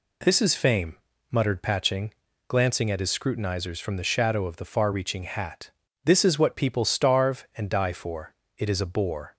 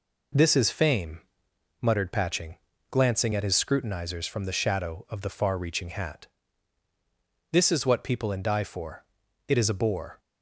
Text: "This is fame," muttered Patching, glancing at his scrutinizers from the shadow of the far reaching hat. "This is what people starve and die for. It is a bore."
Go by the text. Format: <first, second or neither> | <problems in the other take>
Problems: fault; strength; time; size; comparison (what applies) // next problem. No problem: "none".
first | skips "starve"; at 8.3 s